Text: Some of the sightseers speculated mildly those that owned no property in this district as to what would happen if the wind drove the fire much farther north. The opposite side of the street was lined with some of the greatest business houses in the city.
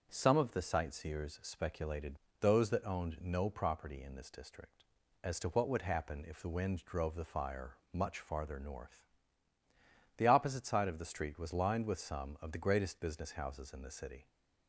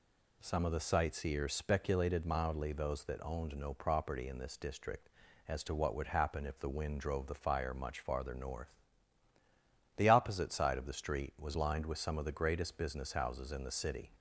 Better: second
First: starts louder than the rest; until 1.1 s; 7 dB // skips "mildly"; at 2.2 s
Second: none

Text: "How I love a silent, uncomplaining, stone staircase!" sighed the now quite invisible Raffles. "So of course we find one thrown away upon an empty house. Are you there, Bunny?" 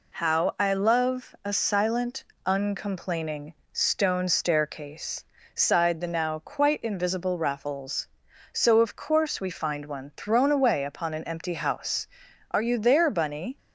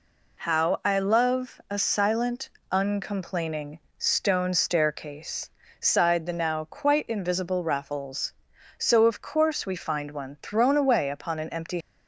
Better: first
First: none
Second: stops before "house Are you there Bunny"; at 11.8 s

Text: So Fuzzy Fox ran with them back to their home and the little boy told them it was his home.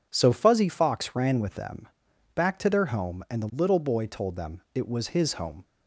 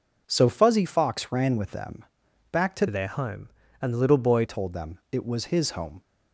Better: first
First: pauses between "them" and "back"; noticeable; at 1.8 s; 0.46 s long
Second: pauses between "them" and "back"; noticeable; at 2.0 s; 0.46 s long // changes voice from "their" to "boy"; from 2.8 to 4.4 s; 1.6 s long

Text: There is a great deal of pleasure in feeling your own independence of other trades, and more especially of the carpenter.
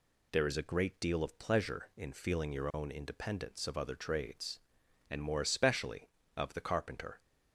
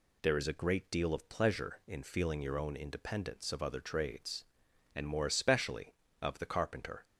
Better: neither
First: none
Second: none

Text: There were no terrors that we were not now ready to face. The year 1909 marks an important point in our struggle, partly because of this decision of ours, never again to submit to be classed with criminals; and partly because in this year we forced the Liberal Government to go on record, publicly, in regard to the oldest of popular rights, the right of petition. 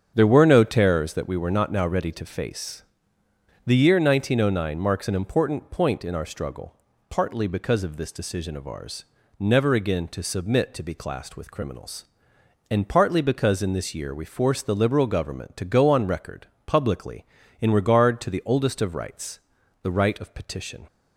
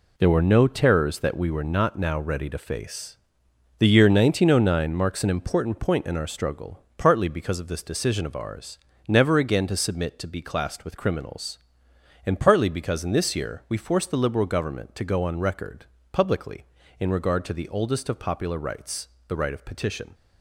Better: second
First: starts louder than the rest; strong; until 1.1 s; 8 dB // skips "popular"; at 18.9 s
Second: none

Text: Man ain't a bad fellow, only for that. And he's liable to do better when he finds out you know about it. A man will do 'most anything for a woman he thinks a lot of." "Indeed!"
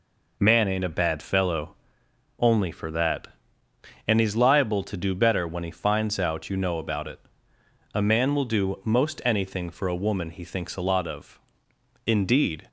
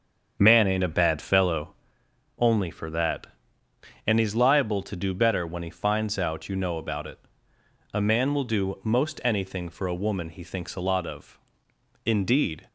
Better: first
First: none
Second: starts louder than the rest; strong; until 1.7 s; 7 dB

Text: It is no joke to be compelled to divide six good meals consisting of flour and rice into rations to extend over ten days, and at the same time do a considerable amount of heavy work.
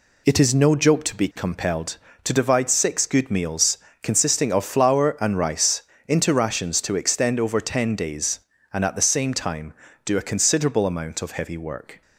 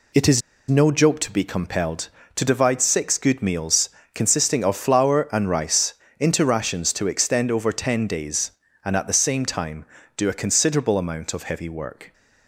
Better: first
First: pauses between "meals" and "consisting"; slight; at 3.7 s; 0.24 s long // pauses between "rice" and "into"; slight; at 5.8 s; 0.26 s long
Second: pauses between "is" and "no"; slight; at 0.4 s; 0.29 s long // pauses between "meals" and "consisting"; slight; at 3.9 s; 0.24 s long // pauses between "rice" and "into"; slight; at 5.9 s; 0.26 s long

